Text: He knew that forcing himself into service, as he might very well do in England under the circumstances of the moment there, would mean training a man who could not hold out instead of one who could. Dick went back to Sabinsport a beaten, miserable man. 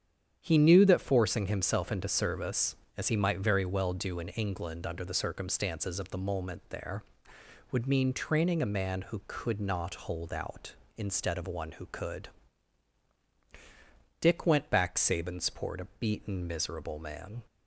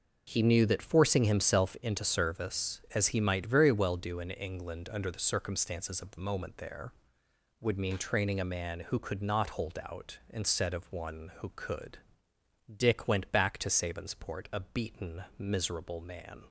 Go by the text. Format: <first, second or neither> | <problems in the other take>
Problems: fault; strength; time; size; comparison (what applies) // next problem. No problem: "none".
second | starts louder than the rest; strong; until 1.4 s; 9 dB // skips "to"; at 14.9 s